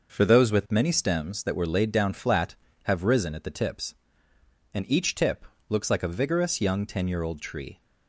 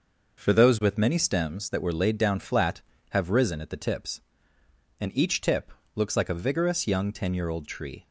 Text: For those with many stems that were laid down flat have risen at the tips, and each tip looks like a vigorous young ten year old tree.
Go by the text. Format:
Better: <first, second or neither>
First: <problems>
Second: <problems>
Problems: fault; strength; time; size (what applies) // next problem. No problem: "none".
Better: neither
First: pauses between "tip" and "looks"; slight; at 5.4 s; 0.24 s long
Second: pauses between "tip" and "looks"; slight; at 5.7 s; 0.24 s long